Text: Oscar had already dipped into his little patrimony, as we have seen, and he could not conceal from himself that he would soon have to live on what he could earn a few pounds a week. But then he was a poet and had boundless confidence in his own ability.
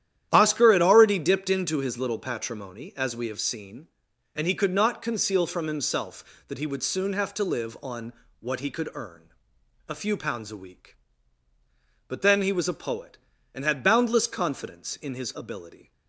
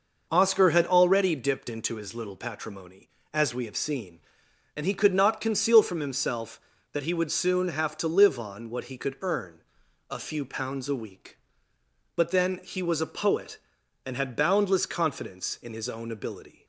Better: second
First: starts louder than the rest; strong; until 1.3 s; 11 dB // pauses between "on" and "what"; slight; at 8.1 s; 0.28 s long // pauses between "earn" and "a"; noticeable; at 9.2 s; 0.64 s long // skips "own"; at 15.3 s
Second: pauses between "earn" and "a"; noticeable; at 9.6 s; 0.48 s long

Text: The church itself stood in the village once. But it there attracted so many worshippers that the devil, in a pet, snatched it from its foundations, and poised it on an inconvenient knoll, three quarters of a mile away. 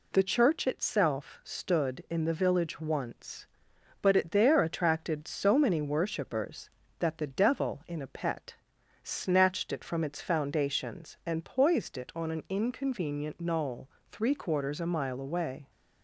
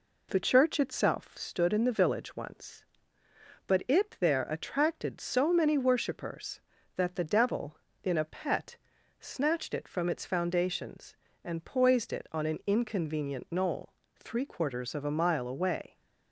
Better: second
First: skips "of"; at 14.8 s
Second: none

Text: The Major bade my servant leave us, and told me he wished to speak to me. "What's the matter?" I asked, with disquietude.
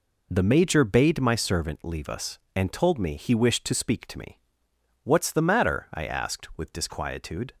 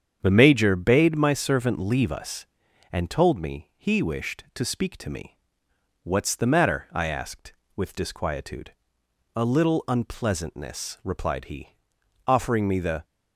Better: first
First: none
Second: starts louder than the rest; strong; until 1.2 s; 8 dB // goes on to say "A little unpleasantness replied he offering me the"; strong; from 9.3 s on; 3.7 s long

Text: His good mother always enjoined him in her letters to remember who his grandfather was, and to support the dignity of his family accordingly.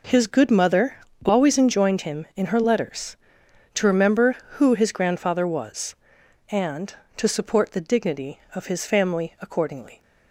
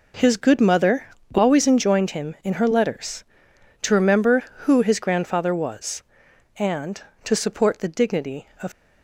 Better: first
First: pauses between "mother" and "always"; slight; at 0.9 s; 0.28 s long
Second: pauses between "mother" and "always"; slight; at 1.0 s; 0.27 s long // stops before "his family accordingly"; at 8.7 s

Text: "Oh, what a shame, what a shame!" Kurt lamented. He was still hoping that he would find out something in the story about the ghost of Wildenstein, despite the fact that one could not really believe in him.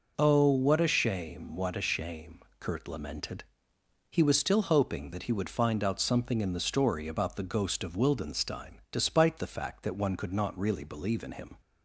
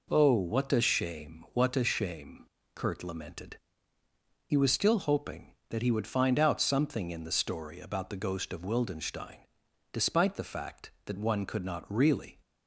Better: first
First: none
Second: stops before "believe in him"; at 12.4 s

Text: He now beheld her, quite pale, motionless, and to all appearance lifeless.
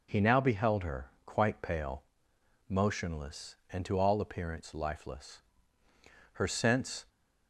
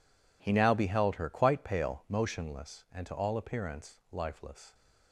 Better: second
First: goes on to say "Her sense"; noticeable; from 6.3 s on; 0.72 s long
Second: none

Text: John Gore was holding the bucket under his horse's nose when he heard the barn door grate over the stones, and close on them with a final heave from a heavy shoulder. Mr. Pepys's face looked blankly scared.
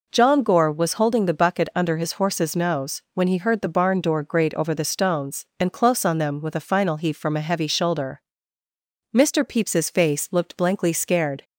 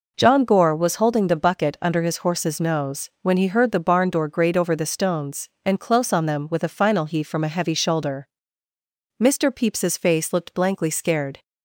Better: neither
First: none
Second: none

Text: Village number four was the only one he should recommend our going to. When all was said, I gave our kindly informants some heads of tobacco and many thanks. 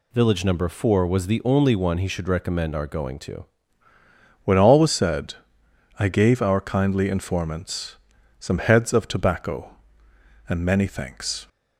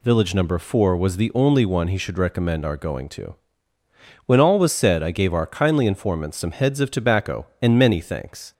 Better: second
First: changes voice at "When"; from 4.4 s on; 7.0 s long // pauses between "informants" and "some"; at 7.9 s; 0.42 s long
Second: none

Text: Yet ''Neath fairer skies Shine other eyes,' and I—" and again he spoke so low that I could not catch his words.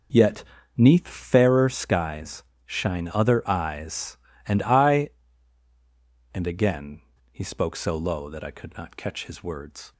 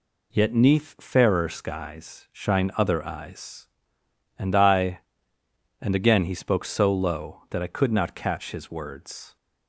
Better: second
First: starts louder than the rest; noticeable; until 1.5 s; 5.5 dB // pauses between "Yet" and "Neath"; slight; at 0.4 s; 0.34 s long // pauses between "skies" and "Shine"; slight; at 2.4 s; 0.22 s long // pauses between "again" and "he"; slight; at 7.0 s; 0.29 s long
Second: none

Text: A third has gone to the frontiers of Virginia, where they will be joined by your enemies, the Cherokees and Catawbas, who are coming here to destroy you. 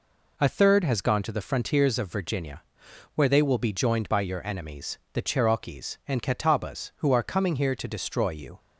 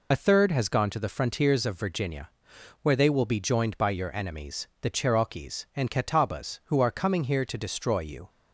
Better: first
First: none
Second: loses the start of "A"; at 0.1 s; 45 ms

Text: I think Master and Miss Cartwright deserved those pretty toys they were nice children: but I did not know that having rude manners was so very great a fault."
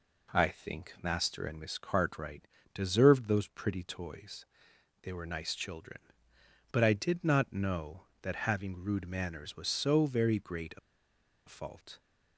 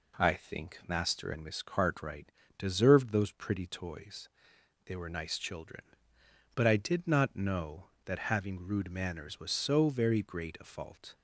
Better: second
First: pauses between "Cartwright" and "deserved"; slight; at 2.4 s; 0.30 s long // pauses between "toys" and "they"; noticeable; at 4.4 s; 0.56 s long // pauses between "a" and "fault"; noticeable; at 10.7 s; 0.68 s long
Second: pauses between "Cartwright" and "deserved"; slight; at 2.2 s; 0.30 s long // pauses between "toys" and "they"; noticeable; at 4.2 s; 0.56 s long

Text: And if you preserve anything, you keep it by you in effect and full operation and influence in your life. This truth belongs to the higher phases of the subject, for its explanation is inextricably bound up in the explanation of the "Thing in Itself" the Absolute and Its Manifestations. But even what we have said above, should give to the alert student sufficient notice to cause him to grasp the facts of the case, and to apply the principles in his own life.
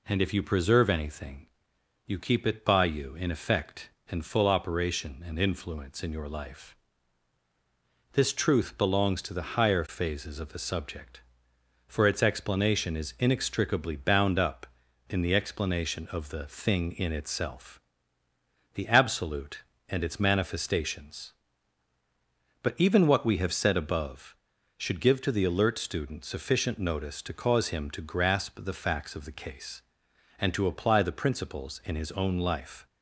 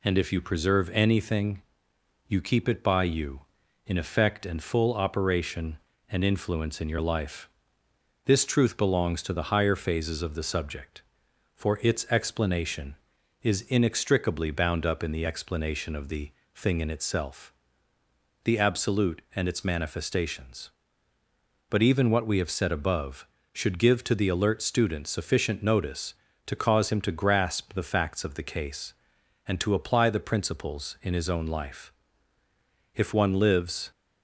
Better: first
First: pauses between "Itself" and "the"; noticeable; at 17.7 s; 0.94 s long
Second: pauses between "the" and "Thing"; slight; at 16.3 s; 0.24 s long // pauses between "Itself" and "the"; noticeable; at 17.5 s; 0.90 s long // goes on to say "If one lives"; noticeable; from 32.9 s on; 0.96 s long

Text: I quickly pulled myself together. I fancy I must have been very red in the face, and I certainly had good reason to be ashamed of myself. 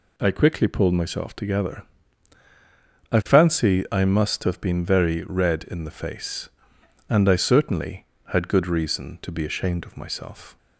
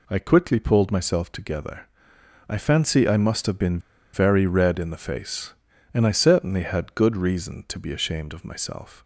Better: first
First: none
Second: pauses between "been" and "very"; slight; at 3.7 s; 0.34 s long

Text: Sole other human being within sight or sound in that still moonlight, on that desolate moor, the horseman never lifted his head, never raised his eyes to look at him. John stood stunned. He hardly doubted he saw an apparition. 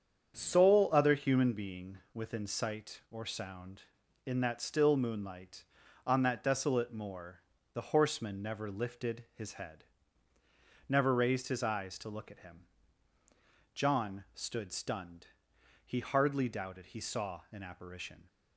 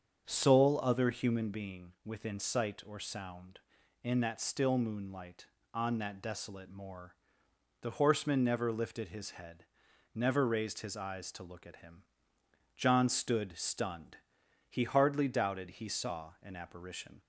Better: neither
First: starts louder than the rest; strong; until 1.3 s; 8 dB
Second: starts louder than the rest; until 1.2 s; 7 dB

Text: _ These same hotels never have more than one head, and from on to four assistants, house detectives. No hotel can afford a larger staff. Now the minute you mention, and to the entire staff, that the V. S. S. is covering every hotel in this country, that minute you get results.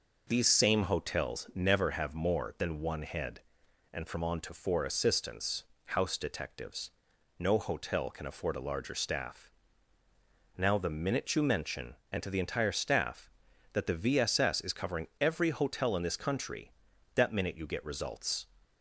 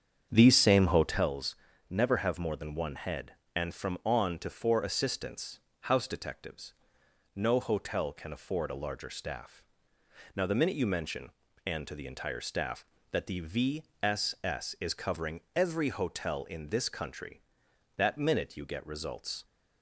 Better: first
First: none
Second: starts louder than the rest; strong; until 1.3 s; 7.5 dB // pauses between "hotels" and "never"; slight; at 1.5 s; 0.34 s long // pauses between "V" and "S"; slight; at 13.8 s; 0.18 s long // pauses between "covering" and "every"; slight; at 15.4 s; 0.16 s long

